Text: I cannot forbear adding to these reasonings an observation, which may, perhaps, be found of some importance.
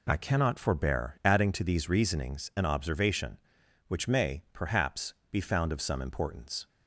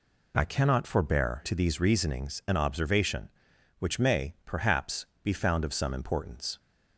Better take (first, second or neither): first